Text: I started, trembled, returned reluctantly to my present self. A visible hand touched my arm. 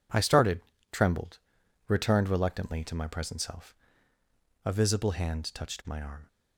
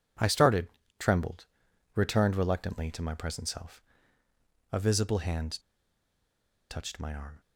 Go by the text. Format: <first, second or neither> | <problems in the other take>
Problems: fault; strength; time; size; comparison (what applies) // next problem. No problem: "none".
first | pauses between "hand" and "touched"; at 5.5 s; 1.1 s long